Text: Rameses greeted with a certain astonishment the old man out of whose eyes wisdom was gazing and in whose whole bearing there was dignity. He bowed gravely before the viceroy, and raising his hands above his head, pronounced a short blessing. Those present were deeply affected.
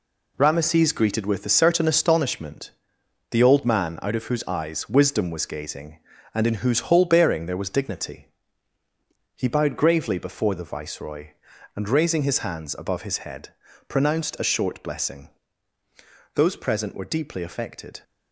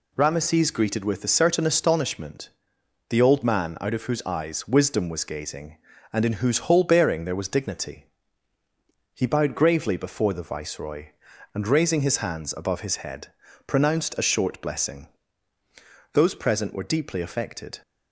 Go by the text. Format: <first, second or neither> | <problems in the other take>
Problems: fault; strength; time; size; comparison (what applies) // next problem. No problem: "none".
second | gets quieter; throughout; 7 dB // pauses between "astonishment" and "the"; noticeable; at 2.7 s; 0.58 s long; noticeable in the second